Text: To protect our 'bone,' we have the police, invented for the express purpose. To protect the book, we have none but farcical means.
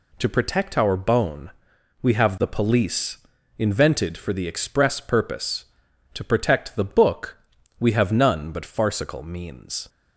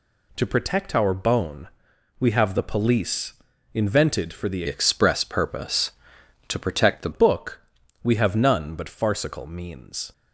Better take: first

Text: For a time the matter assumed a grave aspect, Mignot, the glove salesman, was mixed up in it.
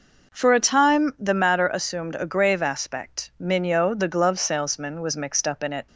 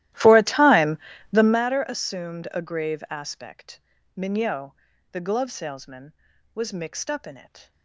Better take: first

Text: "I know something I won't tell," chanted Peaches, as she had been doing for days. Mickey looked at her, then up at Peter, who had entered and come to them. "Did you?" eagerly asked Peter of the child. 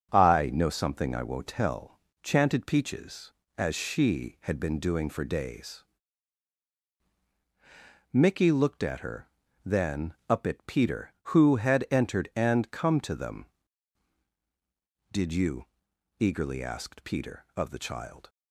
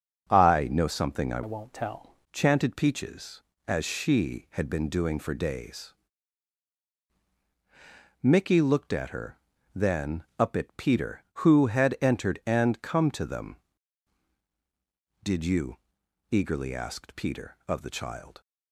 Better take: first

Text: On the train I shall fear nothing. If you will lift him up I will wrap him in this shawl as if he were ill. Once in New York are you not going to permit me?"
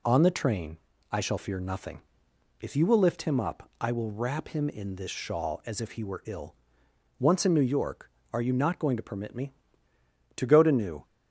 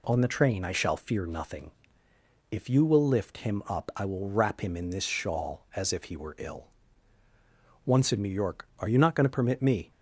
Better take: second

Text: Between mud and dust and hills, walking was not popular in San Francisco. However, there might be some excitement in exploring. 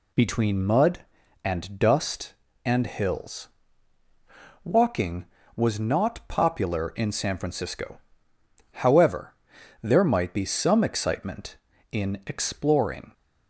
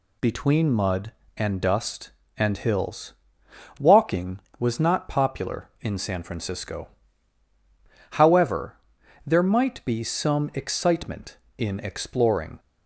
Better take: neither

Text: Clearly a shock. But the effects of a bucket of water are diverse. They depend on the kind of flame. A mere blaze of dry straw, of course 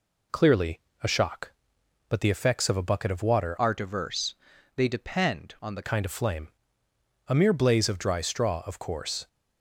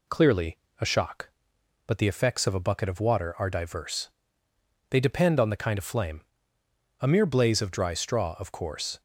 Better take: second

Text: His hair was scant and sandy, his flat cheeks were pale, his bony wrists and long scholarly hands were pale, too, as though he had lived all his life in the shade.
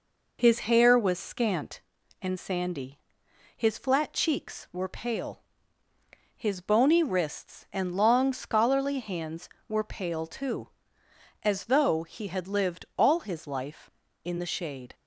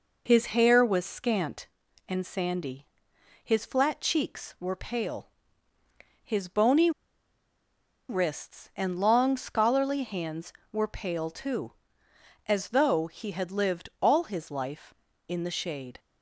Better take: first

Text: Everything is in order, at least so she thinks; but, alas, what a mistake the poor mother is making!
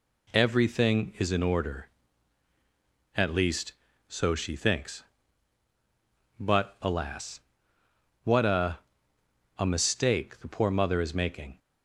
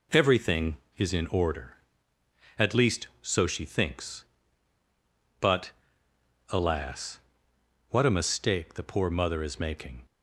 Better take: second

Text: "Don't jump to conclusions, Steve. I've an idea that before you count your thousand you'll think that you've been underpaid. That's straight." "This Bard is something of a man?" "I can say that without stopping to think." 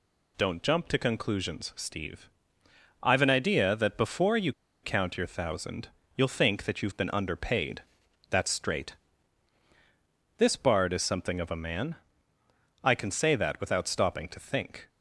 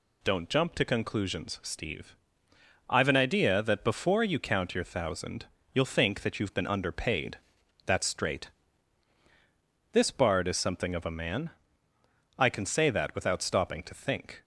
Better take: second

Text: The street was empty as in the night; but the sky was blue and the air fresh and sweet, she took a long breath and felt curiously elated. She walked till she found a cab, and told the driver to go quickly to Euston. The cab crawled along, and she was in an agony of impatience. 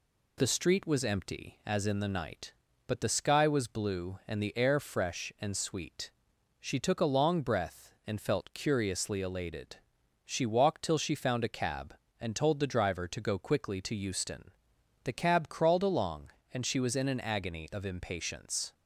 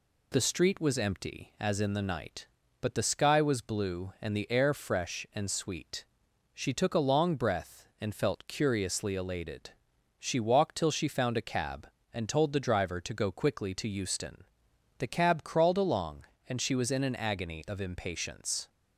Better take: neither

